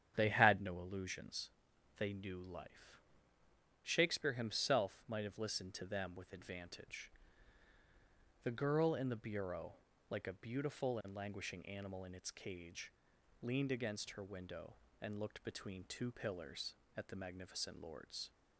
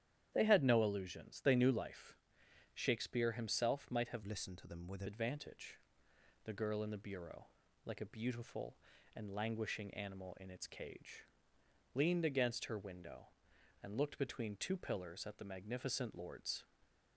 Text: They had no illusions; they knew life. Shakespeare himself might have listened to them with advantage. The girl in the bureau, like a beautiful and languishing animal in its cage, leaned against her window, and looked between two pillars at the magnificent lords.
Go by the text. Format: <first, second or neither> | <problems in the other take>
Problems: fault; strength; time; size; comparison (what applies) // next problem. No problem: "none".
first | starts louder than the rest; strong; until 1.3 s; 10.5 dB; strong in the first // changes voice from "listened" to "with"; from 4.2 to 5.0 s; 0.8 s long